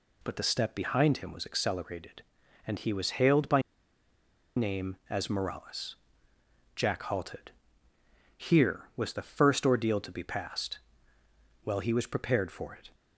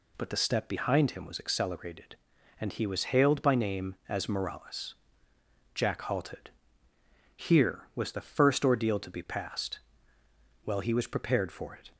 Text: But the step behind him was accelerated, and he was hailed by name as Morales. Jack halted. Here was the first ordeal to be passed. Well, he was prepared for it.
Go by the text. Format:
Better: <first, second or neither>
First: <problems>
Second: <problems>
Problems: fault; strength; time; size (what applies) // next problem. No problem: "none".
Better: second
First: pauses between "by" and "name"; noticeable; at 3.6 s; 0.96 s long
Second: none